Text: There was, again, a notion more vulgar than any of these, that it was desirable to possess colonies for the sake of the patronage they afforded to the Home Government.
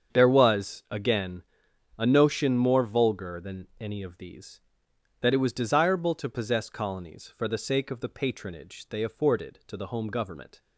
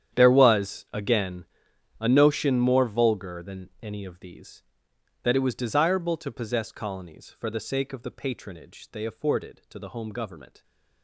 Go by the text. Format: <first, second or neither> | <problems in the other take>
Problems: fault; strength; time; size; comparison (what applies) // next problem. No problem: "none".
first | gets quieter; strong; throughout; 16.5 dB // starts louder than the rest; strong; until 1.2 s; 9.5 dB; strong in the first